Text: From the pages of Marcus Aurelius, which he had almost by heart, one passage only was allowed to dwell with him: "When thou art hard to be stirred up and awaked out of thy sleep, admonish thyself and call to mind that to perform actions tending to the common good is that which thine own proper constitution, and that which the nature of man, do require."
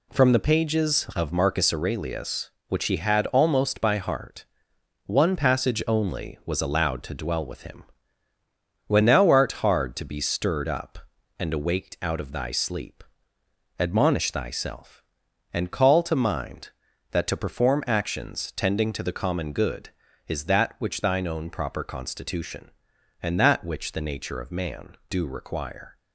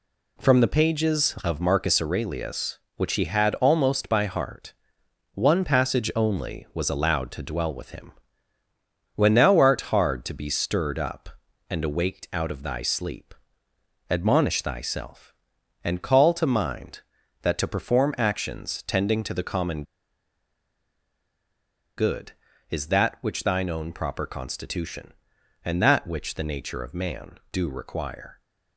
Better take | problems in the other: first | pauses between "common" and "good"; strong; at 19.8 s; 2.1 s long

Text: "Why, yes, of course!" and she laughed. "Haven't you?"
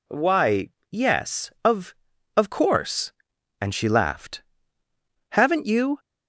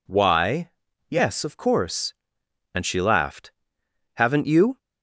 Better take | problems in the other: second | says "of" twice; at 2.3 s

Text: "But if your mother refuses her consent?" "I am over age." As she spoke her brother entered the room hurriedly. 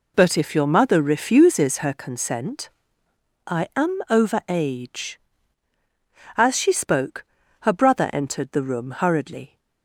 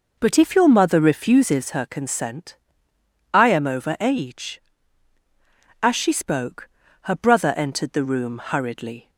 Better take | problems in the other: first | starts louder than the rest; noticeable; until 1.7 s; 5.5 dB // pauses between "spoke" and "her"; slight; at 6.6 s; 0.34 s long; also in the first

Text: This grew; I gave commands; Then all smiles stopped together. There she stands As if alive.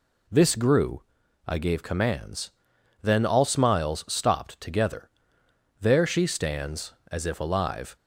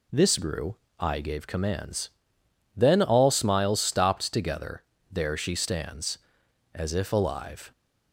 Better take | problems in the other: neither | none

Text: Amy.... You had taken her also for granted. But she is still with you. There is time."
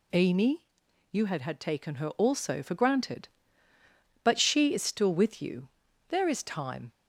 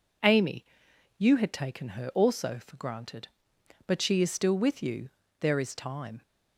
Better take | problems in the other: second | says "had" twice; at 1.4 s

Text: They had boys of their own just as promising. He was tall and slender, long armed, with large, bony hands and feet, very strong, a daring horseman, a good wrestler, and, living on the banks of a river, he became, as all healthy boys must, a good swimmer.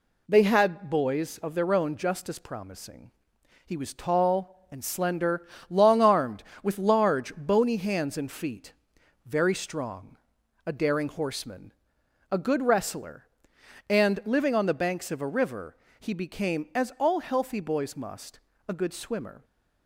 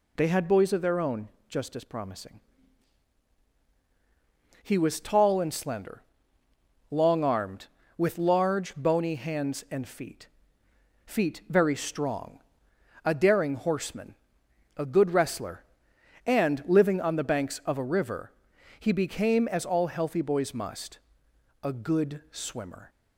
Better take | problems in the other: first | pauses between "own" and "just"; slight; at 1.2 s; 0.20 s long // says "feet" twice; at 11.0 s

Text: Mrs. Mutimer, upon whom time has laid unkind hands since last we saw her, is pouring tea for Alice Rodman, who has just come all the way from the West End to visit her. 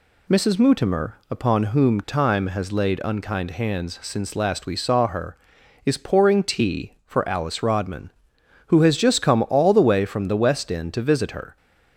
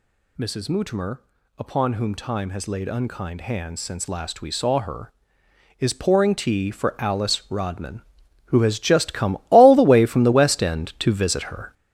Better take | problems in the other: first | gets louder; strong; throughout; 8 dB

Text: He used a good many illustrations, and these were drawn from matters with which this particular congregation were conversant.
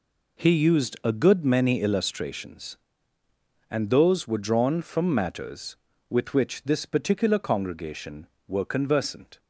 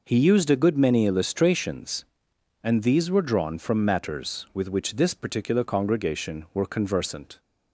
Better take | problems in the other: second | says "those" for "these"; at 3.8 s

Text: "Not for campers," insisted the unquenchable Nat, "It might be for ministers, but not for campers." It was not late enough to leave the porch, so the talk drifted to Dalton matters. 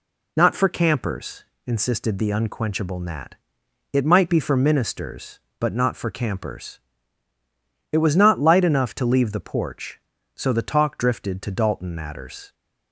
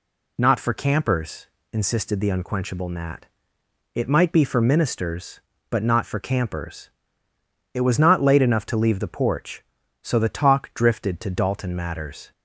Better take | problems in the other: second | says "light" for "late"; at 8.3 s

